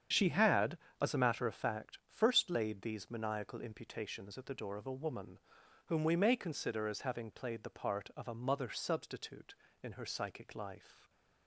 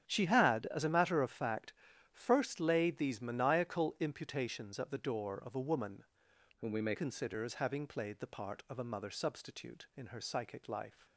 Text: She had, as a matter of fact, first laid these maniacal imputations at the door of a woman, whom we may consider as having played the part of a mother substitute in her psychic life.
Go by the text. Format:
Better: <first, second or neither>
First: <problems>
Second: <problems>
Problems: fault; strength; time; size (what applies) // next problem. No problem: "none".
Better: first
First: starts louder than the rest; strong; until 1.3 s; 8 dB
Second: starts louder than the rest; strong; until 1.0 s; 8.5 dB // changes voice from "whom" to "may"; from 6.5 to 6.9 s; 0.4 s long